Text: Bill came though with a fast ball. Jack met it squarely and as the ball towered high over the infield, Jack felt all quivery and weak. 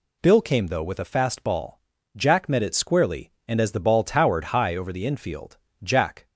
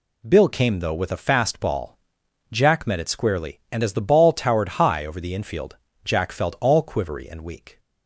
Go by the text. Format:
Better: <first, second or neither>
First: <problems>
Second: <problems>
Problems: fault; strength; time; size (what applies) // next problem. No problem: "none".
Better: second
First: stops before "felt all quivery and weak"; at 6.2 s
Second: none